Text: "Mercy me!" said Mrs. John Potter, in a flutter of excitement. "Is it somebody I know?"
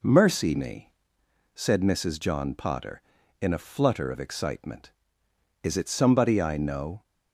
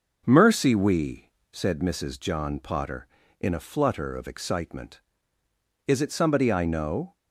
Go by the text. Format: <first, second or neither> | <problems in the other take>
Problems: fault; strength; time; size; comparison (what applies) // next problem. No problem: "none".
first | says "we" for "me"; at 0.7 s